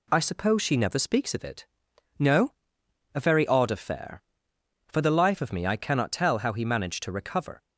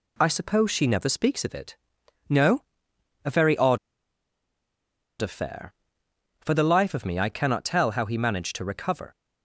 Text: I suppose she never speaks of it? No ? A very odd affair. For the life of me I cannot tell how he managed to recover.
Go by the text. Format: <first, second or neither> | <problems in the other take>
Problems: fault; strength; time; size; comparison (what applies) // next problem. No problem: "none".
first | pauses between "odd" and "affair"; strong; at 3.7 s; 1.4 s long